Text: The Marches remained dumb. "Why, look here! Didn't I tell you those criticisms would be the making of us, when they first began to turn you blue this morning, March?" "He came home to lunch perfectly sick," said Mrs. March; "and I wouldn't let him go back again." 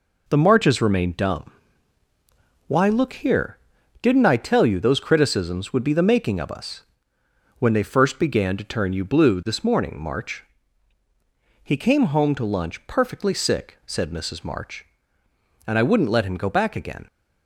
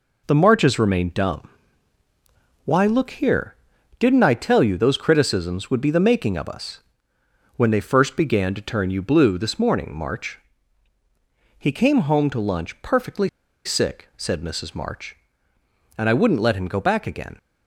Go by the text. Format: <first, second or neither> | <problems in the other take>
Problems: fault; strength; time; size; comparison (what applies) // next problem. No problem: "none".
first | pauses between "perfectly" and "sick"; at 13.2 s; 0.37 s long